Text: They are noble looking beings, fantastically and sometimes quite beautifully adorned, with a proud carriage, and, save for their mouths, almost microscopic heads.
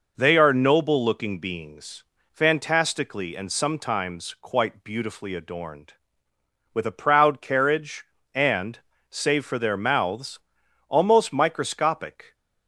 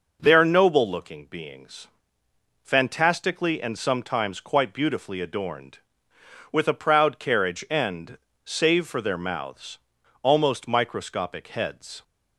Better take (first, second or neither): second